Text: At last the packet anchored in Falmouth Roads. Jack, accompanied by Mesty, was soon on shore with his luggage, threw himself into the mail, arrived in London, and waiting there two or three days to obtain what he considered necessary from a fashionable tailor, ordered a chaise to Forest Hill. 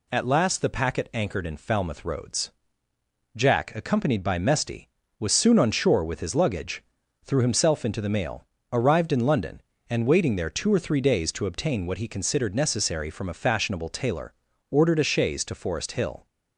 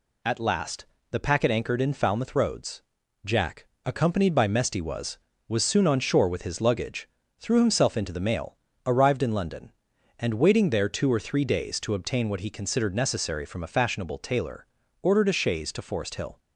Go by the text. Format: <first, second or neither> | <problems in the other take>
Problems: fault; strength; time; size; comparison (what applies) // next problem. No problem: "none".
first | pauses between "last" and "the"; slight; at 0.8 s; 0.26 s long // says "was" twice; at 5.4 s